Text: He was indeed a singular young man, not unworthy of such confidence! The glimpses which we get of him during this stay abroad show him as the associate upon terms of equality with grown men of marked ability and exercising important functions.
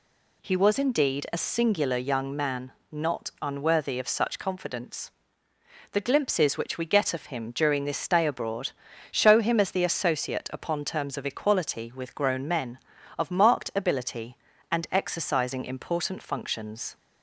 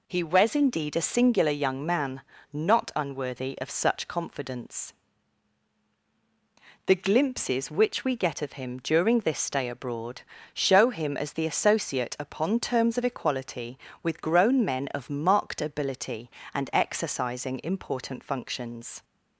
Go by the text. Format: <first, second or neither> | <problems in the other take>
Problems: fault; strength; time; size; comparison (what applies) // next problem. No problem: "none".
neither | pauses between "abroad" and "show"; the same in both